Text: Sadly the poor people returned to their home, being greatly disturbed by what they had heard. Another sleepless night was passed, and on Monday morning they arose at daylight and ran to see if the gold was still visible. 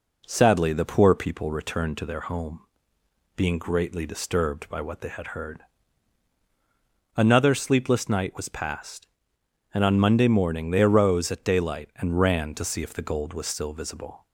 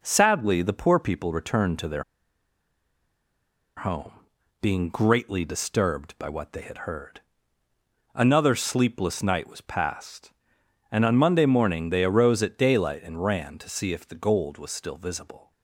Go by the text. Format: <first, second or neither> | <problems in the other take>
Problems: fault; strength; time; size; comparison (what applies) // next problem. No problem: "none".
first | pauses between "their" and "home"; strong; at 2.0 s; 1.7 s long